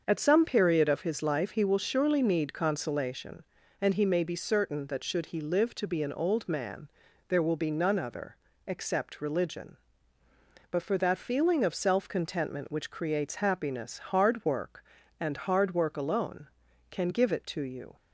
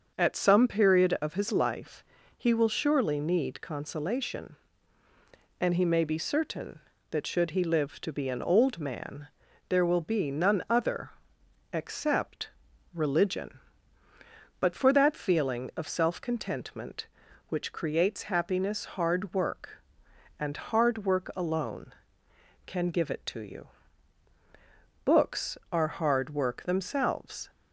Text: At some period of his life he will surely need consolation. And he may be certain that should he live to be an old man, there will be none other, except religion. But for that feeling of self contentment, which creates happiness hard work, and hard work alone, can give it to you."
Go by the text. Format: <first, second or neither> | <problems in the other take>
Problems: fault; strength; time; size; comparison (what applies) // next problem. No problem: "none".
first | starts louder than the rest; until 1.1 s; 6.5 dB; also in the first // pauses between "life" and "he"; slight; at 2.0 s; 0.34 s long // pauses between "except" and "religion"; at 12.4 s; 0.44 s long // goes on to say "Books are hard work themselves"; strong; from 25.0 s on; 2.4 s long